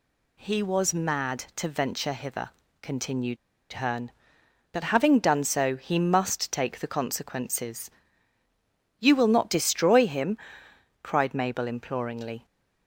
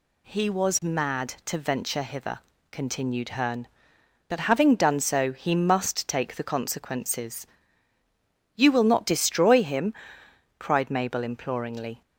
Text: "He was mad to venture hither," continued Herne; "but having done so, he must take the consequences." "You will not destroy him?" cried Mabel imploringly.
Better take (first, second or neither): second